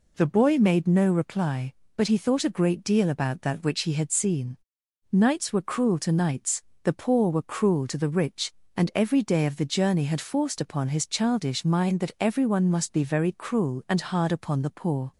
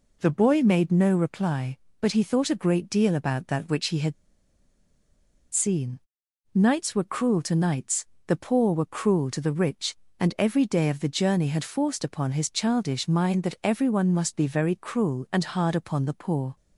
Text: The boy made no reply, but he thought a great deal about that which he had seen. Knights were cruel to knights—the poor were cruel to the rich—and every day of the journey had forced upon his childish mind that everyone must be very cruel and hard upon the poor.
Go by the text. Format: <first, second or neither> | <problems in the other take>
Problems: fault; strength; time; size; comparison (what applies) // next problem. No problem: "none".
first | pauses between "had" and "seen"; strong; at 4.1 s; 1.3 s long